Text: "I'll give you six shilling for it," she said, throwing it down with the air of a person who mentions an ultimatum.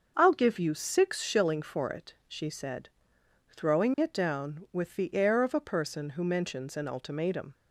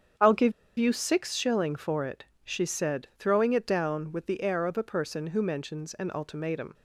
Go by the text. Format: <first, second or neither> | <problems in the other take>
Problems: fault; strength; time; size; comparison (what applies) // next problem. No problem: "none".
first | starts louder than the rest; strong; until 1.4 s; 8 dB; also in the first // pauses between "give" and "you"; slight; at 0.5 s; 0.27 s long